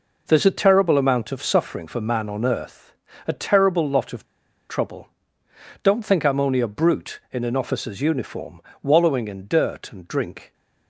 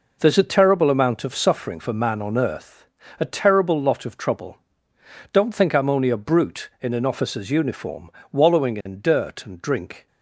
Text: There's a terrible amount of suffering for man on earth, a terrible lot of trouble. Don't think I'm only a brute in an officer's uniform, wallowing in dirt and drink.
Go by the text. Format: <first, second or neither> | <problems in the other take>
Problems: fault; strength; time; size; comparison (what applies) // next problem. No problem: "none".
second | pauses between "of" and "trouble"; at 4.2 s; 0.44 s long